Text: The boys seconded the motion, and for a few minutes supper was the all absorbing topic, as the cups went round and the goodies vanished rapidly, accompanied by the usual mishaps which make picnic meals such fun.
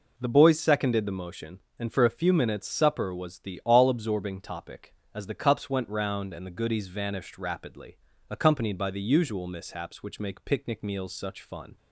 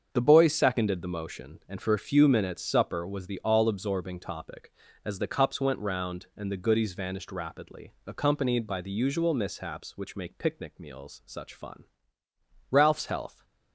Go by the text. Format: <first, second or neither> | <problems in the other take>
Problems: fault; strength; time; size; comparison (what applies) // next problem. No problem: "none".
first | starts louder than the rest; until 1.1 s; 7 dB // goes on to say "Ralph's health"; noticeable; from 12.7 s on; 0.74 s long